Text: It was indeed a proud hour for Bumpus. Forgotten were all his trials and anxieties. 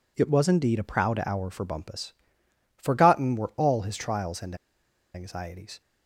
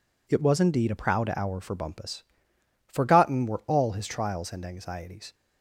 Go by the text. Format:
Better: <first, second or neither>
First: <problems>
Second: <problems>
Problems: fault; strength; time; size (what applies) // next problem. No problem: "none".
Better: second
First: pauses between "and" and "anxieties"; noticeable; at 4.5 s; 0.58 s long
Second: none